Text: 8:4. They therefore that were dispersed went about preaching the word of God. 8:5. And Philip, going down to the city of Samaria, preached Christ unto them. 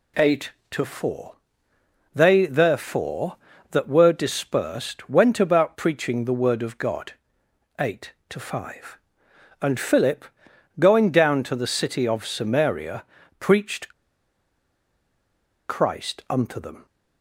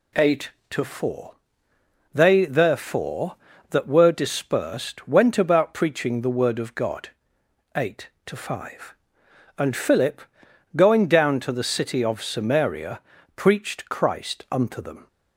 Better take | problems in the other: second | pauses between "preached" and "Christ"; strong; at 13.9 s; 1.7 s long

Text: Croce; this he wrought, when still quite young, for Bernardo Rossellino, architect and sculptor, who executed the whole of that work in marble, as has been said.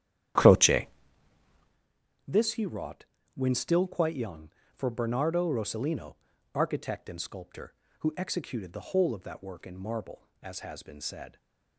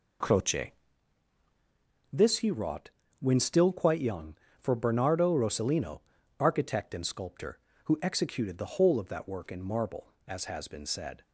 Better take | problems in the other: second | starts louder than the rest; strong; until 1.9 s; 11 dB

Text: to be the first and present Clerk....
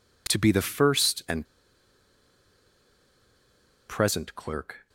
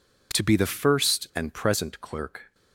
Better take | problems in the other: second | pauses between "and" and "present"; strong; at 1.4 s; 2.4 s long

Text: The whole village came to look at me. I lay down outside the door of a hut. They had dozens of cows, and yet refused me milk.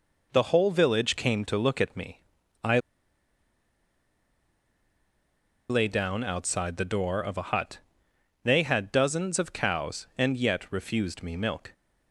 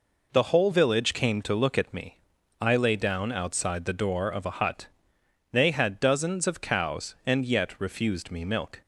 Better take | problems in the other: second | pauses between "I" and "lay"; strong; at 2.7 s; 2.8 s long

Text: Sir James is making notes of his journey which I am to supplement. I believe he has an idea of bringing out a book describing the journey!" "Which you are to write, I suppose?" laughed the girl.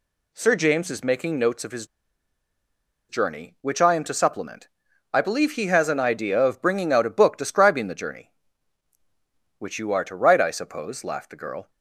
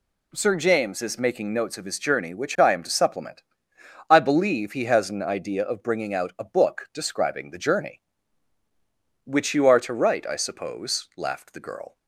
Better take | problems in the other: second | pauses between "his" and "journey"; at 1.8 s; 1.2 s long

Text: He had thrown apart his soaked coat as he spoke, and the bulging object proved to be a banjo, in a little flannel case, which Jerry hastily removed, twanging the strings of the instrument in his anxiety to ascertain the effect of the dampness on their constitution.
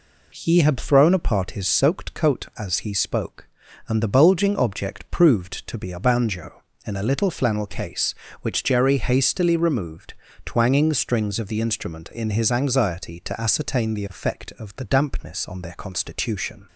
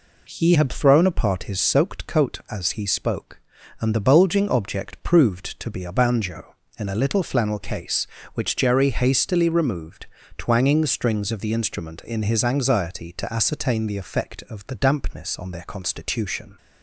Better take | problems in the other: neither | none

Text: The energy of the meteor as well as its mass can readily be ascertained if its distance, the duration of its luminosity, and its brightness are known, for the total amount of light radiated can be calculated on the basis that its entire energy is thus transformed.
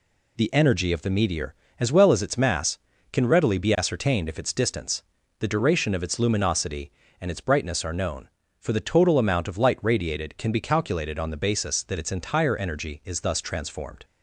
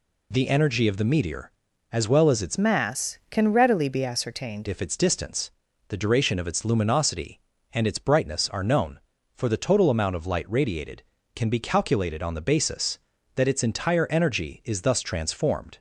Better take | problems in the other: first | changes voice from "mass" to "ascertained"; from 2.5 to 4.6 s; 2.1 s long

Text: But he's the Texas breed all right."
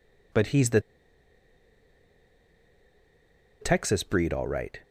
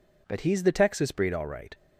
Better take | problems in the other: second | pauses between "the" and "Texas"; strong; at 0.8 s; 2.8 s long

